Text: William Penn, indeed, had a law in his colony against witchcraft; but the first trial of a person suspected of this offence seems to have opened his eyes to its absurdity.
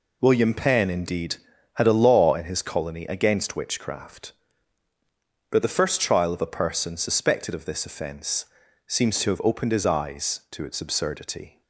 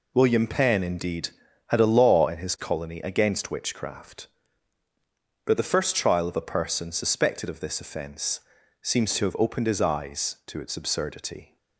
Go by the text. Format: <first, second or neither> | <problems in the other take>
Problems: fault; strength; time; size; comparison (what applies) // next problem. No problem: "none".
neither | pauses between "offence" and "seems"; the same in both